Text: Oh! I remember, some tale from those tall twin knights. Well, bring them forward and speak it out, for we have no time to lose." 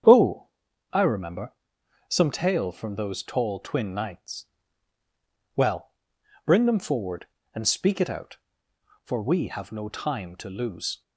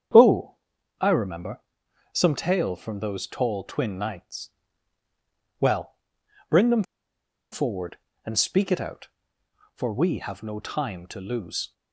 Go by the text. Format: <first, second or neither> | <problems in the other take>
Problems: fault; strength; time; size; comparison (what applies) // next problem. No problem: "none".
first | starts louder than the rest; strong; until 1.5 s; 8 dB; strong in the first // pauses between "them" and "forward"; noticeable; at 6.8 s; 0.67 s long